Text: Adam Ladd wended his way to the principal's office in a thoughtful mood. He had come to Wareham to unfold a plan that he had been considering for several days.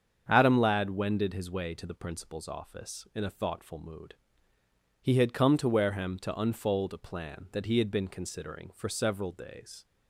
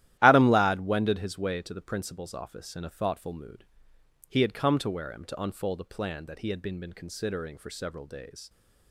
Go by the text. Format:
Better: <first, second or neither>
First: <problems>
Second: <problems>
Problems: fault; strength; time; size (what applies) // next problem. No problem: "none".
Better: first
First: starts louder than the rest; strong; until 1.2 s; 7.5 dB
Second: starts louder than the rest; strong; until 1.2 s; 13.5 dB // says "been" twice; at 6.7 s